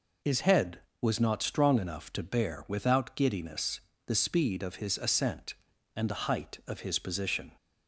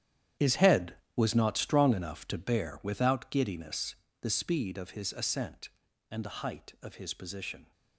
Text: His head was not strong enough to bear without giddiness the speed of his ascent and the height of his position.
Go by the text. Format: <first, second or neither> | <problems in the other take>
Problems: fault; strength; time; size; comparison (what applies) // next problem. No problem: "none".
first | gets quieter; strong; throughout; 13.5 dB // pauses between "giddiness" and "the"; slight; at 3.9 s; 0.26 s long; slight in the first